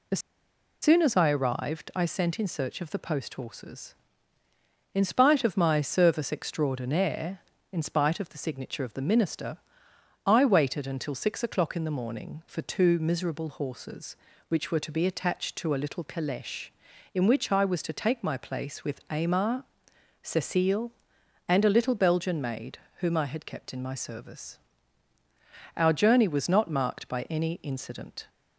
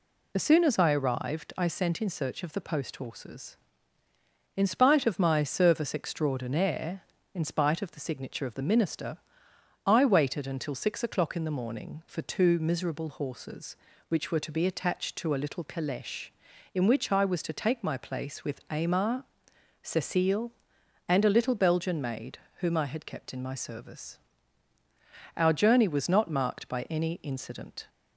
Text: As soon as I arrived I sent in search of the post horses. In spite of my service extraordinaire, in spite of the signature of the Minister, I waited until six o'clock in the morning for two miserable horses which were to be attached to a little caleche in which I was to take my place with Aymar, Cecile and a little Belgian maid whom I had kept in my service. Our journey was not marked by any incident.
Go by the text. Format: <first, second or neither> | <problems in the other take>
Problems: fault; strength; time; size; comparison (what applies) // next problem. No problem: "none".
second | pauses between "As" and "soon"; noticeable; at 0.1 s; 0.62 s long // pauses between "maid" and "whom"; slight; at 22.7 s; 0.20 s long; slight in the second